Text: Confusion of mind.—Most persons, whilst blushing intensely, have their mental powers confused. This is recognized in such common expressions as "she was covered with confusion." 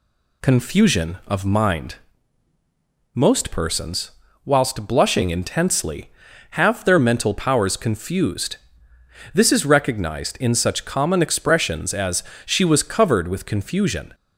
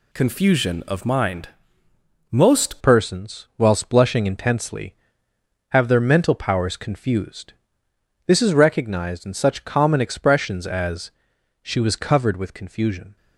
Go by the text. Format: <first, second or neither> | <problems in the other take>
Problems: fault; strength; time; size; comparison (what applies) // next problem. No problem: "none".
first | changes voice at "persons"; from 2.8 s on; 10.3 s long // pauses between "as" and "she"; noticeable; at 11.1 s; 0.50 s long; slight in the first